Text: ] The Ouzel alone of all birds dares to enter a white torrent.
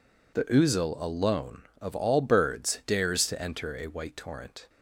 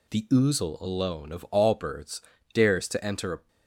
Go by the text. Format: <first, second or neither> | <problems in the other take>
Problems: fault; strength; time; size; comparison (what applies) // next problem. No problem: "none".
first | pauses between "birds" and "dares"; slight; at 2.2 s; 0.32 s long // stops before "white torrent"; at 3.4 s